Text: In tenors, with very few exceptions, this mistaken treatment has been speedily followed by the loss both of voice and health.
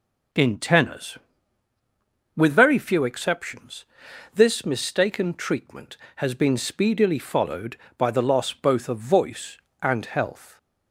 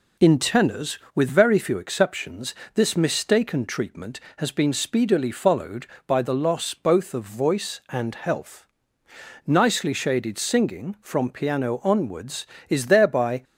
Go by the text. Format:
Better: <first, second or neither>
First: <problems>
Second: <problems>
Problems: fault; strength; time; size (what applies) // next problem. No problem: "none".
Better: first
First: none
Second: goes on to say "Nicely shaded singing from piano onwards is thereby"; strong; from 9.4 s on; 3.9 s long